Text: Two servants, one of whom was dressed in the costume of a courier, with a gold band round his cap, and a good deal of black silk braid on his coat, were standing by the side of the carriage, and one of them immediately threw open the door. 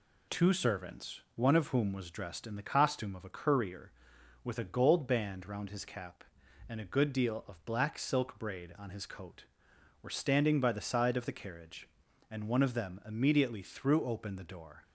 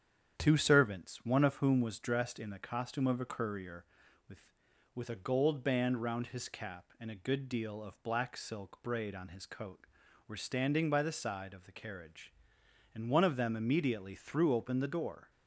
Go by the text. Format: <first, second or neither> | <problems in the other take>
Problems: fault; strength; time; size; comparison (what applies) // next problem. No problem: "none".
first | starts louder than the rest; strong; until 1.4 s; 8.5 dB // says "with" twice; at 4.9 s